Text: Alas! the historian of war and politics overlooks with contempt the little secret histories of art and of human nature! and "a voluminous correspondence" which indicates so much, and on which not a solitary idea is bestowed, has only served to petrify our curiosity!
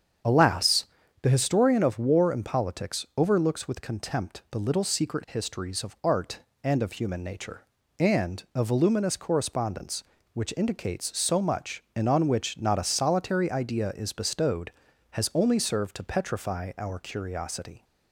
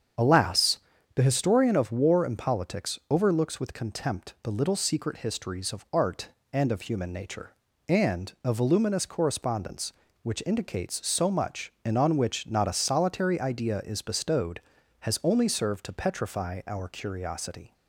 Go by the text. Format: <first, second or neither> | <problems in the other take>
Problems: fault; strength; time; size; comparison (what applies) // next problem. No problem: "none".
neither | starts louder than the rest; strong; the same in both